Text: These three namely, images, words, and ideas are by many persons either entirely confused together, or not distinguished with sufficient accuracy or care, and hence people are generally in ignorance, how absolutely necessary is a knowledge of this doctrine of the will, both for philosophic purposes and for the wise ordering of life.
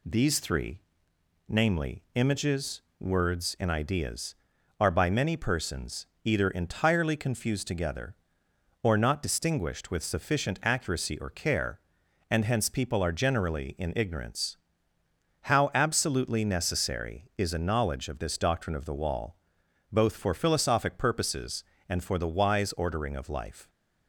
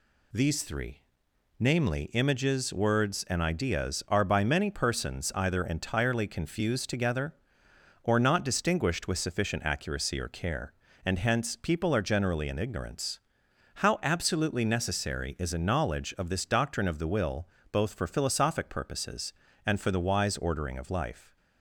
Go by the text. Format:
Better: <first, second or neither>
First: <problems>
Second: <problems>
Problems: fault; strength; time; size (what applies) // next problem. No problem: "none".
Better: second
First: pauses between "three" and "namely"; noticeable; at 0.8 s; 0.70 s long // pauses between "persons" and "either"; slight; at 6.0 s; 0.18 s long // says "wall" for "will"; at 18.9 s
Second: pauses between "three" and "namely"; noticeable; at 0.9 s; 0.60 s long